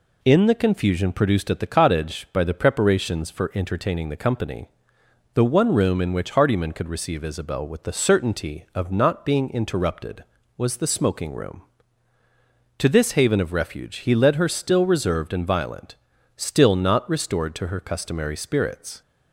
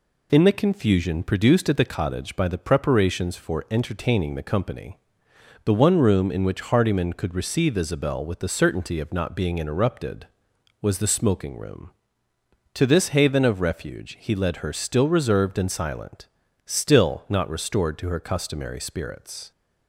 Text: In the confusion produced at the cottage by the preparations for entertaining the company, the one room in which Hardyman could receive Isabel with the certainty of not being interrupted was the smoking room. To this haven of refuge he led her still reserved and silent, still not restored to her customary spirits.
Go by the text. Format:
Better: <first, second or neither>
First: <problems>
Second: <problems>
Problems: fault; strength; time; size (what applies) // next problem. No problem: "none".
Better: second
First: says "violent" for "silent"; at 15.4 s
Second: none